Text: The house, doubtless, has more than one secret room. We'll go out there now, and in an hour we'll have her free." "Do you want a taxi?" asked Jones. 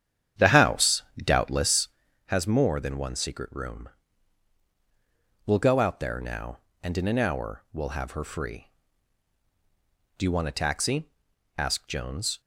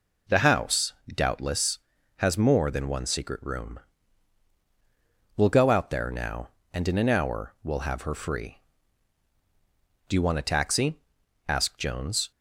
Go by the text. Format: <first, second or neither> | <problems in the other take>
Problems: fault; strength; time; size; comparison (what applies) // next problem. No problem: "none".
second | starts louder than the rest; strong; until 2.3 s; 9.5 dB